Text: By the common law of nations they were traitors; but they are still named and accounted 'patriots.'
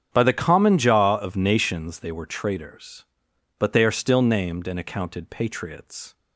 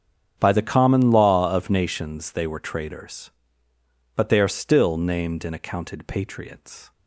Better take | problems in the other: second | starts louder than the rest; strong; until 1.1 s; 8 dB; strong in the second // says "jaw" for "law"; at 0.7 s

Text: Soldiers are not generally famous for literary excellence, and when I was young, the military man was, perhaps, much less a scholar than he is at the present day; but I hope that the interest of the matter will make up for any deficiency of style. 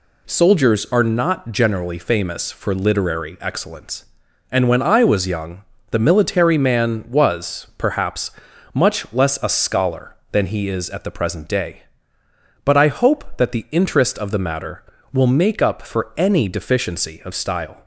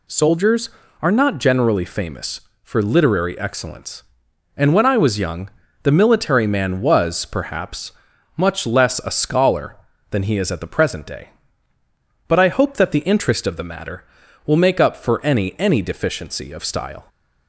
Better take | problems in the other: first | says "any" twice; at 15.5 s

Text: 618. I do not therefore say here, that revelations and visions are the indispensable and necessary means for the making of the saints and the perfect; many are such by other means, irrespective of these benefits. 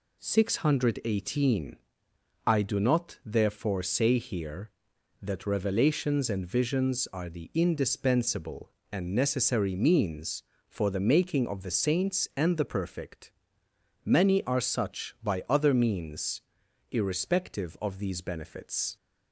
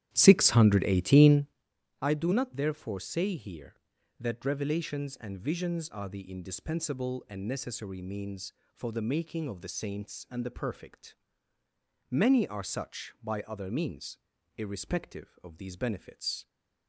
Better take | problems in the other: first | starts louder than the rest; strong; until 1.7 s; 11.5 dB

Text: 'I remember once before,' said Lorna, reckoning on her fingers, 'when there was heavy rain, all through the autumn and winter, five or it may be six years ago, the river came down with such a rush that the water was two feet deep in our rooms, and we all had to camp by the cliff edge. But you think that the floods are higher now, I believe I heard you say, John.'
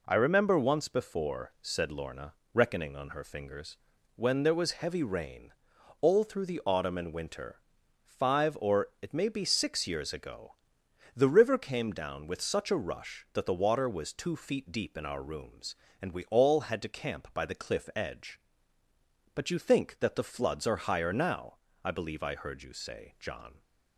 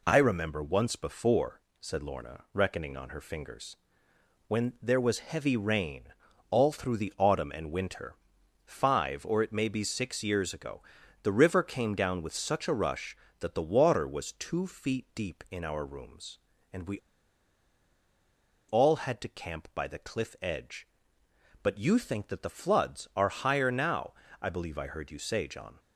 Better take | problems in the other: first | pauses between "we" and "all"; strong; at 16.9 s; 1.6 s long

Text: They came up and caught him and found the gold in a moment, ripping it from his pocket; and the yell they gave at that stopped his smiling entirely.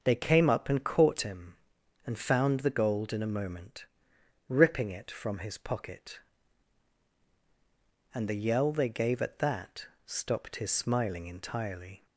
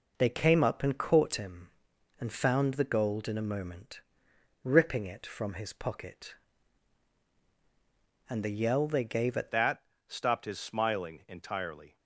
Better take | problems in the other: first | changes voice at "that"; from 9.5 s on; 2.4 s long // pauses between "that" and "stopped"; slight; at 9.8 s; 0.26 s long; slight in the first

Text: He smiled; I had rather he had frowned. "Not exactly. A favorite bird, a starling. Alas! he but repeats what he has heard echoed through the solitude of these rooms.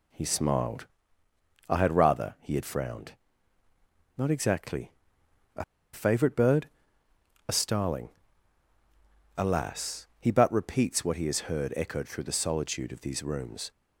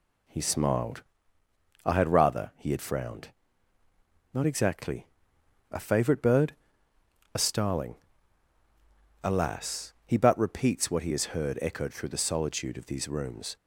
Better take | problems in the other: second | pauses between "A" and "favorite"; slight; at 5.6 s; 0.29 s long

